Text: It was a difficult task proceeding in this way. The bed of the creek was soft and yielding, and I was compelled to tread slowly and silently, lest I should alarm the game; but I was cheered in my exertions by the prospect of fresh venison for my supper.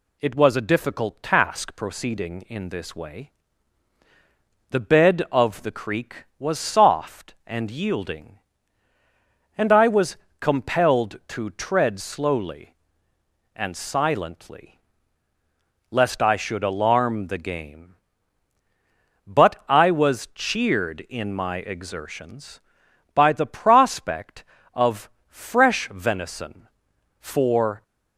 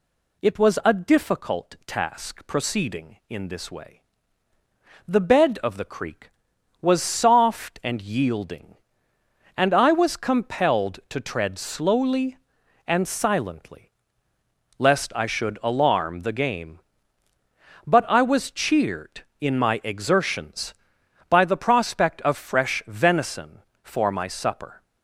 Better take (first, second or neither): second